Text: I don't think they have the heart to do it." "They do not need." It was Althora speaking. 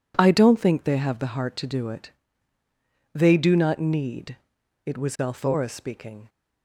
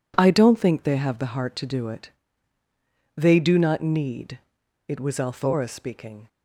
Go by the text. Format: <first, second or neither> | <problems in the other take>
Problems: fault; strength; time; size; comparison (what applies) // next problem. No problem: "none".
neither | none